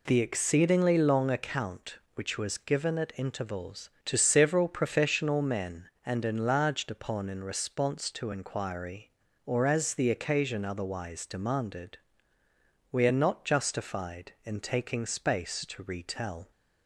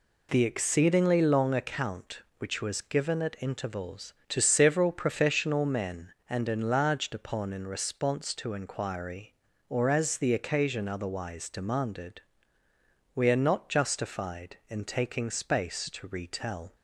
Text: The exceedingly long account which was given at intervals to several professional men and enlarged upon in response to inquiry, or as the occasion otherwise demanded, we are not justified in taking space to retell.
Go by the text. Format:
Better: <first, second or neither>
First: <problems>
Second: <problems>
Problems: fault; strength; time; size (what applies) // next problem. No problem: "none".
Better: neither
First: none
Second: none